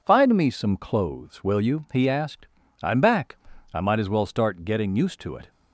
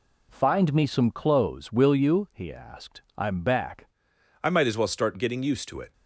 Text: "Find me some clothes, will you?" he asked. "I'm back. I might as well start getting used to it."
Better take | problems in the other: first | changes voice at "I"; from 4.4 s on; 1.5 s long

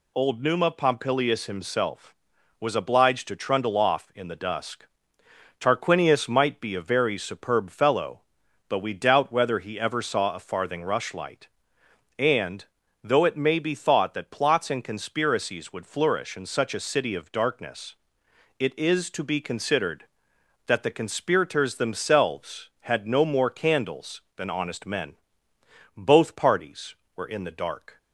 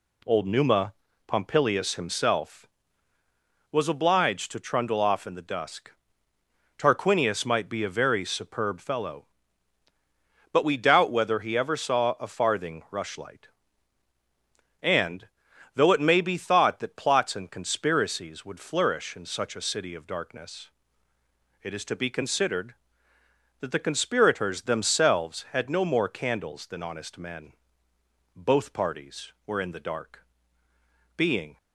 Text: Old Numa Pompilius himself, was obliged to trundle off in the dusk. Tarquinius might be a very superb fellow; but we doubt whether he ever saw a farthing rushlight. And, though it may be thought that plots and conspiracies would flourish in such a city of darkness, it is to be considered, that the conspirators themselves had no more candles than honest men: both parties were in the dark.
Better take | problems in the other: first | pauses between "Numa" and "Pompilius"; slight; at 0.9 s; 0.34 s long // goes on to say "Being"; slight; from 31.1 s on; 0.40 s long

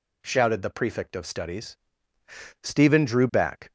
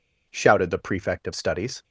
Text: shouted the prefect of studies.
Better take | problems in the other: second | goes on to say "Stephen drew back"; noticeable; from 2.6 s on; 1.0 s long

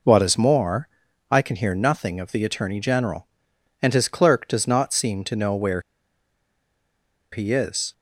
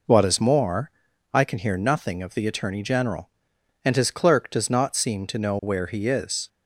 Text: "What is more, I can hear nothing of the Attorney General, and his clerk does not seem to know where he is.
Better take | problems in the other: second | pauses between "where" and "he"; strong; at 5.8 s; 1.5 s long

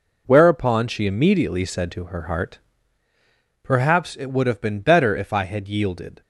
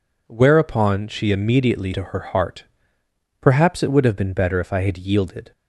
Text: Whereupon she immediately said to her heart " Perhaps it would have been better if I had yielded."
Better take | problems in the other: first | skips "said"; at 1.9 s

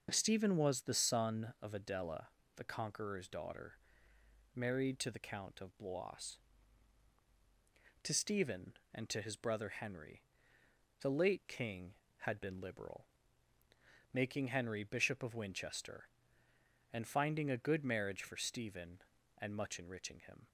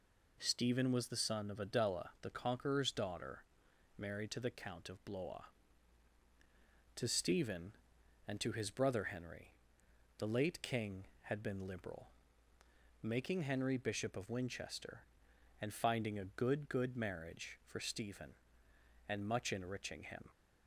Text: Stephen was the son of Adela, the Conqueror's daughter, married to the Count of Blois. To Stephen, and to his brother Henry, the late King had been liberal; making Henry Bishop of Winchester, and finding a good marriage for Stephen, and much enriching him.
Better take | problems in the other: first | says "good" twice; at 16.6 s

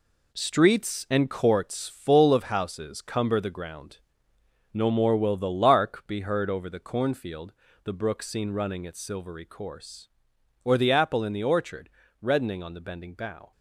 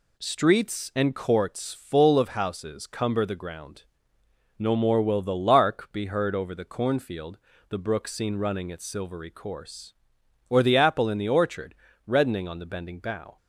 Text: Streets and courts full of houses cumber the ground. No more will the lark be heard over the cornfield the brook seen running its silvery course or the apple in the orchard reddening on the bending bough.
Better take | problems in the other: second | gets quieter; strong; throughout; 8 dB // pauses between "cornfield" and "the"; slight; at 7.5 s; 0.32 s long; slight in the second // pauses between "orchard" and "reddening"; slight; at 11.8 s; 0.32 s long; slight in the second

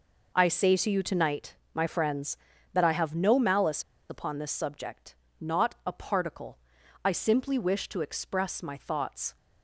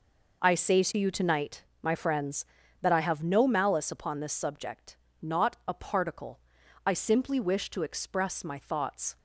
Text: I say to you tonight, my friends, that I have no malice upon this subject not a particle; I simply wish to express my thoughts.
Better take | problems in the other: second | pauses between "malice" and "upon"; slight; at 3.8 s; 0.27 s long // pauses between "subject" and "not"; slight; at 5.1 s; 0.28 s long; slight in the second

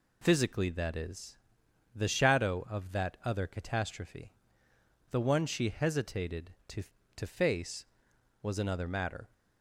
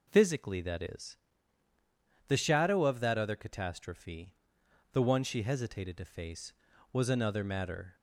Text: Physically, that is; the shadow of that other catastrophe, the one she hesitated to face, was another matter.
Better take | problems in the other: second | says "to" twice; at 7.1 s

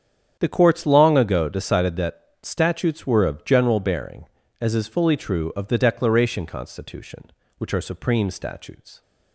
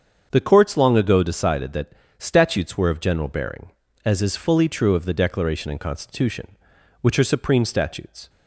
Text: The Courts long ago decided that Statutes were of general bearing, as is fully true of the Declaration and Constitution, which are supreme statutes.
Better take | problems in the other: second | starts louder than the rest; strong; until 1.4 s; 8.5 dB; strong in the second // pauses between "that" and "Statutes"; slight; at 2.2 s; 0.20 s long; slight in the second // skips "and"; at 6.4 s

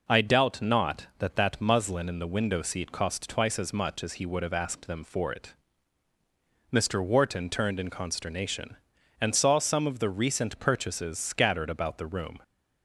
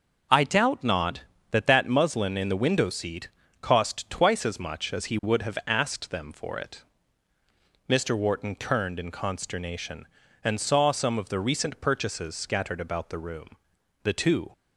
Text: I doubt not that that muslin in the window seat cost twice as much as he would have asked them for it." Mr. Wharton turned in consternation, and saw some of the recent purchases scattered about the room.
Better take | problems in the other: first | starts louder than the rest; until 1.6 s; 6 dB // pauses between "seat" and "cost"; slight; at 3.2 s; 0.32 s long // goes on to say "The two"; slight; from 14.0 s on; 0.48 s long

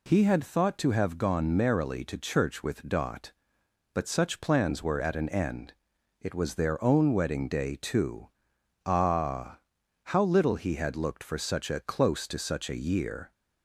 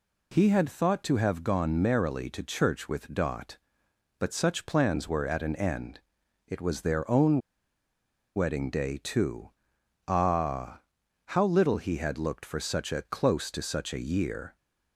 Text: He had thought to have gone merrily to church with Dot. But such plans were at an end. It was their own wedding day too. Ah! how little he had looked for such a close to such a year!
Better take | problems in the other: first | pauses between "own" and "wedding"; noticeable; at 7.3 s; 0.97 s long

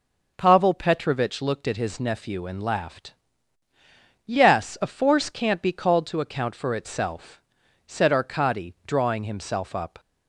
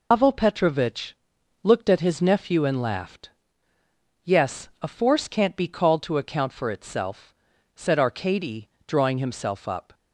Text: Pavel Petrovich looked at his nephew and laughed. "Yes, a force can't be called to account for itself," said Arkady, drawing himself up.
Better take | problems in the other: first | loses the start of "Pavel"; at 0.1 s; 140 ms // pauses between "Petrovich" and "looked"; noticeable; at 1.1 s; 0.48 s long

